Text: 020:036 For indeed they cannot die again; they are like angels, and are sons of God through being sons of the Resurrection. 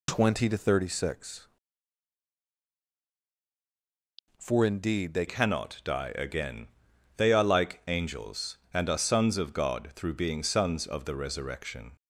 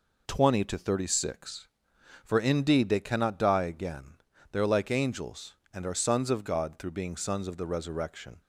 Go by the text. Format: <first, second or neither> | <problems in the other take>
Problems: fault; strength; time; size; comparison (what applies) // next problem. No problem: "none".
second | changes voice at "cannot"; from 5.2 s on; 6.7 s long